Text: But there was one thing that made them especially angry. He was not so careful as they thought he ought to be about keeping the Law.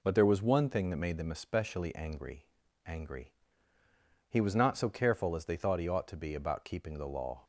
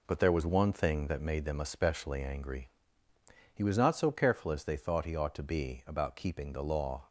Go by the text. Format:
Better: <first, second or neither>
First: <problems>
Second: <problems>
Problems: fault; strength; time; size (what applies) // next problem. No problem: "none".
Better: second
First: says "angry" twice; at 2.8 s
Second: none